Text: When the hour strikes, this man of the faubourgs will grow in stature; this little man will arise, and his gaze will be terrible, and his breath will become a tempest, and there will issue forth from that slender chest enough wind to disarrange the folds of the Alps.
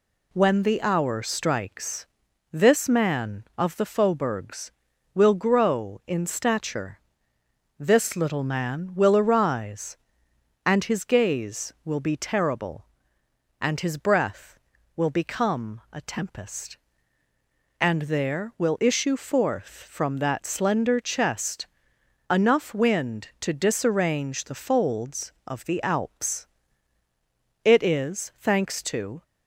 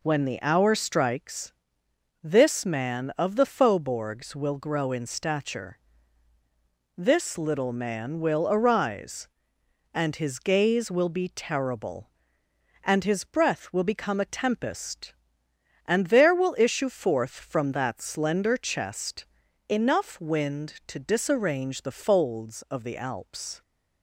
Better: second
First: pauses between "chest" and "enough"; noticeable; at 21.6 s; 0.64 s long // goes on to say "It is thanks to"; from 27.6 s on; 1.6 s long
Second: pauses between "chest" and "enough"; at 19.2 s; 0.42 s long

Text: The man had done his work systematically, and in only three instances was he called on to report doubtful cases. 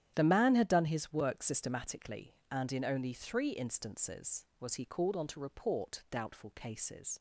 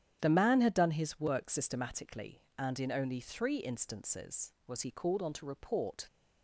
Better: first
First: starts louder than the rest; strong; until 1.1 s; 10.5 dB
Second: starts louder than the rest; strong; until 1.2 s; 9.5 dB // stops before "doubtful cases"; at 6.0 s

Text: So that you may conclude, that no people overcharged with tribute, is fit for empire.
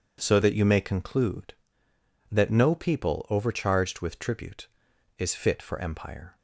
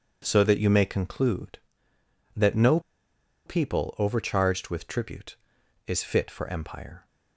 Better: first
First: none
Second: pauses between "no" and "people"; noticeable; at 2.7 s; 0.66 s long

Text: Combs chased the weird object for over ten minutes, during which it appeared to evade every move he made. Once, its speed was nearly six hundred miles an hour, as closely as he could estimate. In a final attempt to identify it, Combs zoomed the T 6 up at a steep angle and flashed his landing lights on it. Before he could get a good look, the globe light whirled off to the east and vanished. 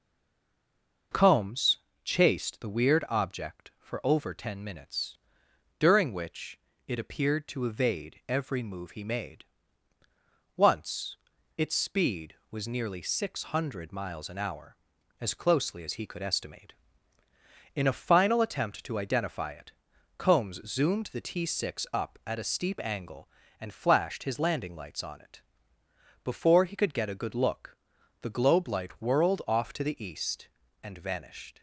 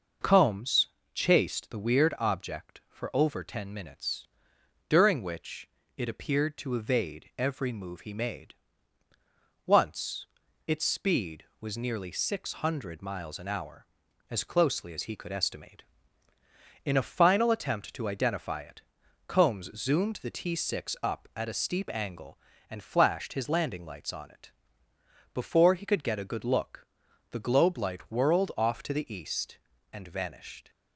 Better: second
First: stays silent before the first word; until 1.1 s; 1.1 s long // pauses between "Combs" and "chased"; slight; at 1.7 s; 0.28 s long // pauses between "which" and "it"; slight; at 6.5 s; 0.28 s long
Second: pauses between "Combs" and "chased"; slight; at 0.8 s; 0.28 s long // pauses between "which" and "it"; slight; at 5.6 s; 0.28 s long

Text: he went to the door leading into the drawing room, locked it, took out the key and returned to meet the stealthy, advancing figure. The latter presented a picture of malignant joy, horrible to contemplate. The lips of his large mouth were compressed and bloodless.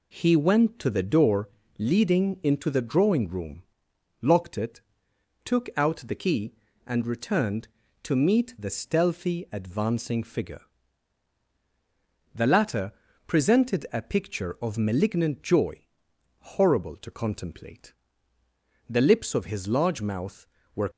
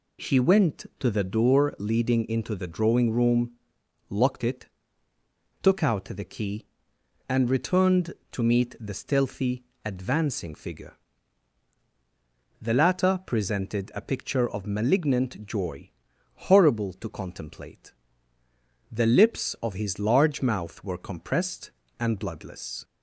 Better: second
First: pauses between "door" and "leading"; slight; at 1.4 s; 0.30 s long // pauses between "latter" and "presented"; at 12.9 s; 0.38 s long // stops before "compressed and bloodless"; at 20.9 s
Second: none

